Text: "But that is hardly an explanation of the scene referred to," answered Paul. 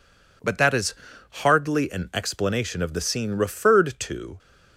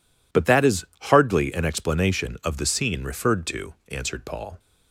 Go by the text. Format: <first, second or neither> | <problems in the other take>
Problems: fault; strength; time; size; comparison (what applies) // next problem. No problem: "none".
second | pauses between "is" and "hardly"; slight; at 0.9 s; 0.36 s long; slight in the second // stops before "answered Paul"; at 4.3 s